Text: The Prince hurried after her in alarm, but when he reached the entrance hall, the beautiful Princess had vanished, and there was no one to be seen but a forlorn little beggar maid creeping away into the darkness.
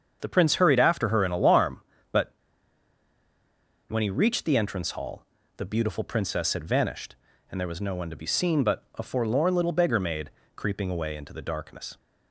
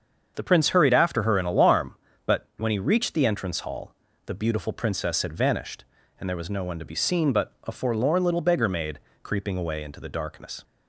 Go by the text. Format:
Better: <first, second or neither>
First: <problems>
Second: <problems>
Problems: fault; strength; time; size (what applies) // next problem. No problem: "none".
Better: second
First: starts louder than the rest; until 1.2 s; 7 dB // pauses between "but" and "when"; strong; at 2.3 s; 1.5 s long // pauses between "maid" and "creeping"; slight; at 10.3 s; 0.24 s long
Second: starts louder than the rest; until 1.3 s; 7 dB // pauses between "maid" and "creeping"; slight; at 8.9 s; 0.22 s long